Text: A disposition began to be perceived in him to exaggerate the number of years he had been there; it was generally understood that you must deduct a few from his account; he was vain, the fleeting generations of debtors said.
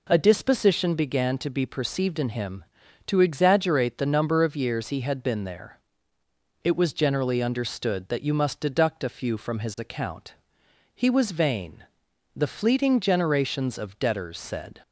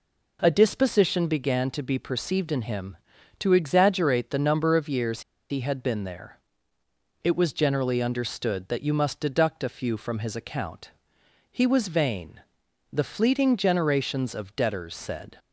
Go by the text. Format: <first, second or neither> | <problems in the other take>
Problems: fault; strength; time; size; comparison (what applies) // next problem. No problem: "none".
first | pauses between "years" and "he"; slight; at 5.2 s; 0.29 s long